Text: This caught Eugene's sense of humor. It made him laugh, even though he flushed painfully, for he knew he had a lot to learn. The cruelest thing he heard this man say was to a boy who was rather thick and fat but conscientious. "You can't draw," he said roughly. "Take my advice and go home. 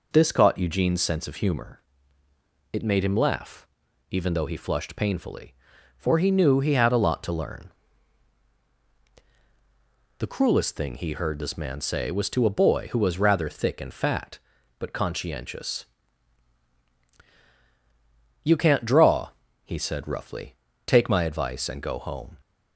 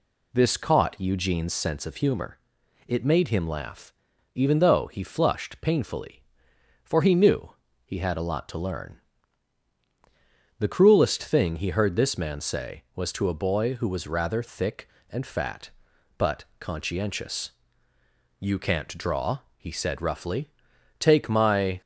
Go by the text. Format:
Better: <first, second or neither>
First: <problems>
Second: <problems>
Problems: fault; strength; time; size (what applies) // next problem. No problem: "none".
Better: first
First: none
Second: pauses between "knew" and "he"; slight; at 7.5 s; 0.34 s long // pauses between "but" and "conscientious"; slight; at 16.4 s; 0.16 s long // stops before "advice and go home"; at 21.8 s